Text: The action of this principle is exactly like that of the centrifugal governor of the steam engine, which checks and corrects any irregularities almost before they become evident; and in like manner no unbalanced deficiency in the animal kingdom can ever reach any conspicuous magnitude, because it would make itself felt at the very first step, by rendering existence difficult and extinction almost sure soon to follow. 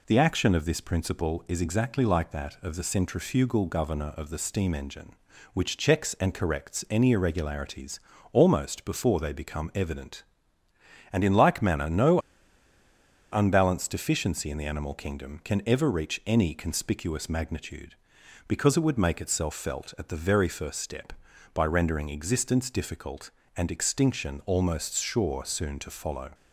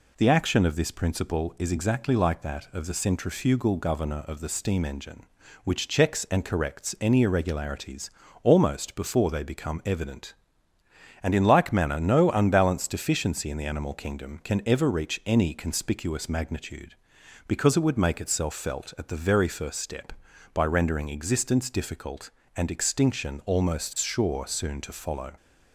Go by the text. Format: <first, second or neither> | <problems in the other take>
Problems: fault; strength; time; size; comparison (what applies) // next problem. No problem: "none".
second | pauses between "irregularities" and "almost"; slight; at 8.0 s; 0.32 s long; slight in the second // pauses between "no" and "unbalanced"; at 12.1 s; 1.1 s long